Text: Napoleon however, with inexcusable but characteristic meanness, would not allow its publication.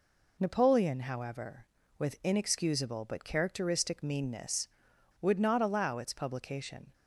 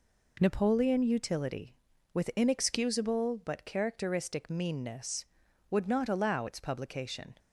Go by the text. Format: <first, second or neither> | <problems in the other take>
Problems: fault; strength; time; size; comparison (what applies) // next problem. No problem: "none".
first | says "utility" for "however"; at 1.0 s